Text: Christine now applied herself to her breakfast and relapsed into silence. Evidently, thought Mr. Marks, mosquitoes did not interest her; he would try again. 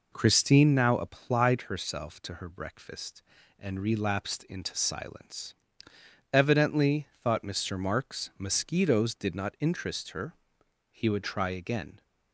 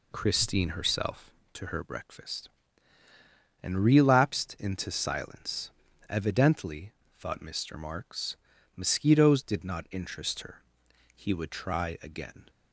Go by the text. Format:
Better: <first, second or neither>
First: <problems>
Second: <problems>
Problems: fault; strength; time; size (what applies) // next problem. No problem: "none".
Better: first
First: none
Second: skips "now applied"; at 0.7 s